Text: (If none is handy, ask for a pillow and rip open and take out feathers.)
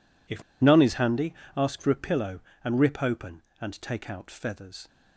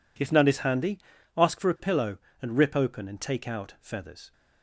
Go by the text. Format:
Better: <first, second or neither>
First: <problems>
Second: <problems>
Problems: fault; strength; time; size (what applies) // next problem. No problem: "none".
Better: second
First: pauses between "If" and "none"; slight; at 0.4 s; 0.18 s long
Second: none